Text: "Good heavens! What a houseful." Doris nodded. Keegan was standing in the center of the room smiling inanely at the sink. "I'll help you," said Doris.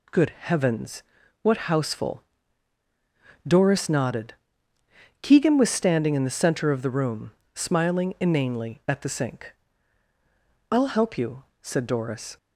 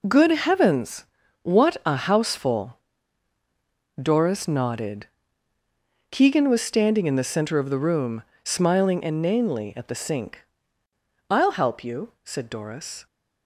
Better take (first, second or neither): second